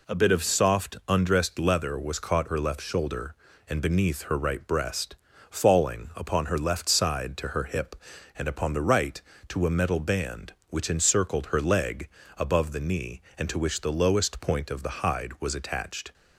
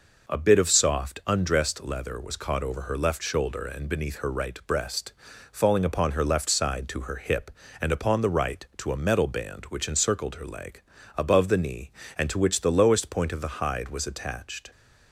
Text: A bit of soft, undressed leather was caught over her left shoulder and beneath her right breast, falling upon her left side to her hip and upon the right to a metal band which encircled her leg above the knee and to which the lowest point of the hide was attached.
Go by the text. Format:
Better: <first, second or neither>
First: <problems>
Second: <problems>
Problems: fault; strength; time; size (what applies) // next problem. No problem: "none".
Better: second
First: skips "over"; at 2.4 s // pauses between "leg" and "above"; slight; at 12.0 s; 0.30 s long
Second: pauses between "leg" and "above"; slight; at 10.8 s; 0.34 s long